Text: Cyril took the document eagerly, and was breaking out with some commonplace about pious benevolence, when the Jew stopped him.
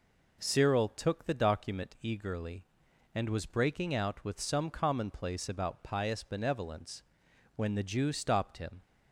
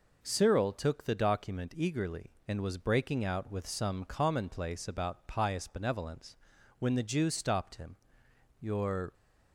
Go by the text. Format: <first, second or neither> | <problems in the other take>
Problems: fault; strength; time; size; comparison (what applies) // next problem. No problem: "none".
first | goes on to say "Your"; from 8.5 s on; 0.54 s long